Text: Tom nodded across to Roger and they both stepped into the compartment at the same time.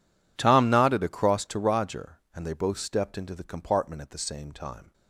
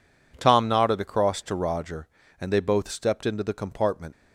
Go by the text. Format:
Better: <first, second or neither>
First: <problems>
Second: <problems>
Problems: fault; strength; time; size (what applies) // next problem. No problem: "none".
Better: first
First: none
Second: stops before "at the same time"; at 4.1 s